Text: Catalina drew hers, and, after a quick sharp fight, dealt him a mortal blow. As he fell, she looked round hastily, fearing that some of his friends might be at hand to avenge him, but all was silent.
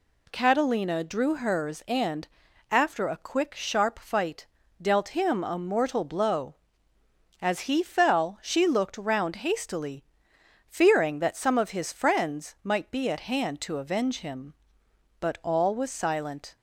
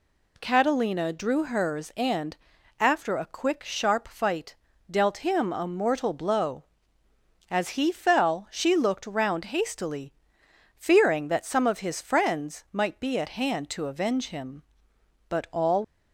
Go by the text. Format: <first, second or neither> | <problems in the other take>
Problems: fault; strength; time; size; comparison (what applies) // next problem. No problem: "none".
first | stops before "was silent"; at 15.8 s